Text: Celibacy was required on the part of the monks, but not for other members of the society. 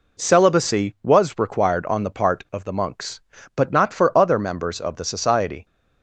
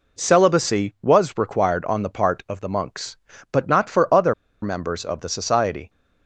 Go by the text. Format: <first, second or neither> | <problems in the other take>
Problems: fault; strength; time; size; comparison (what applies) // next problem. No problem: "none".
first | pauses between "other" and "members"; slight; at 4.3 s; 0.29 s long